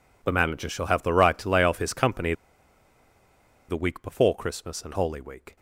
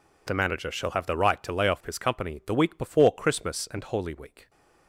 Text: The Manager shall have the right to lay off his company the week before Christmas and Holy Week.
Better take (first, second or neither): second